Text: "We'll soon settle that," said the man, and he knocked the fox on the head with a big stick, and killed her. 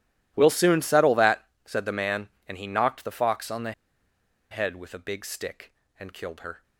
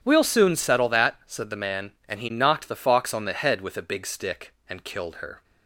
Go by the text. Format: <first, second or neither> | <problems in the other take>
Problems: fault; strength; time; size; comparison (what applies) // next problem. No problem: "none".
second | pauses between "the" and "head"; noticeable; at 3.7 s; 0.79 s long